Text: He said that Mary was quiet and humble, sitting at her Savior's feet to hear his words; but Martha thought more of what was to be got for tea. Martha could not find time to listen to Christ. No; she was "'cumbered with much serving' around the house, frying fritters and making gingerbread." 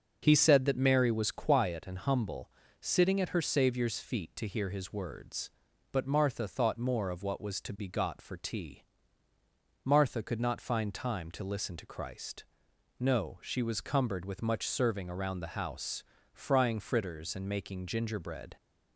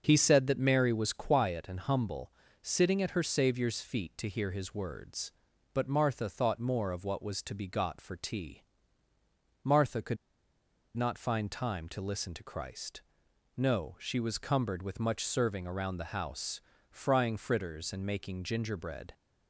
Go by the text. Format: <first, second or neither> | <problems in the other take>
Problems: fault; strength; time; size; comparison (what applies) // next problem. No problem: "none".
first | starts louder than the rest; until 1.0 s; 6 dB; noticeable in the first // pauses between "could" and "not"; noticeable; at 10.1 s; 0.80 s long